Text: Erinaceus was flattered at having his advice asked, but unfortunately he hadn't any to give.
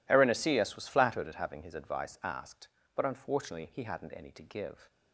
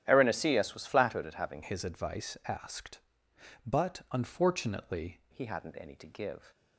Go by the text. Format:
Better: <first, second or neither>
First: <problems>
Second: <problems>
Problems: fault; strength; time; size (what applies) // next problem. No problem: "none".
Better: first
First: none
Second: starts louder than the rest; strong; until 1.0 s; 11.5 dB // changes voice from "his" to "unfortunately"; from 1.6 to 5.2 s; 3.6 s long